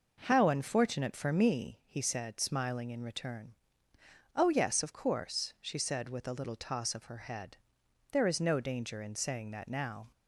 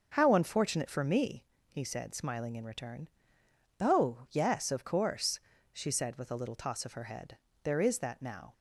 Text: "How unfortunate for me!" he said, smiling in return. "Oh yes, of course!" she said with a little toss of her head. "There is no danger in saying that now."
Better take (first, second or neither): first